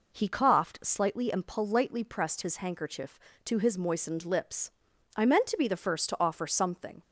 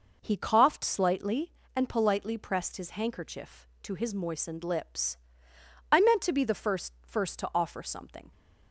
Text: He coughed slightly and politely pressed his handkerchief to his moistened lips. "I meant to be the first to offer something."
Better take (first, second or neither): first